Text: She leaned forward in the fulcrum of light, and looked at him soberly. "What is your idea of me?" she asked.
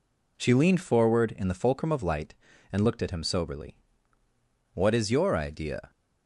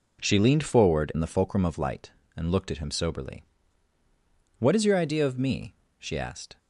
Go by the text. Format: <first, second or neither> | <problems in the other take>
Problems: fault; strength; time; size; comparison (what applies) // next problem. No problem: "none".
second | stops before "of me she asked"; at 5.8 s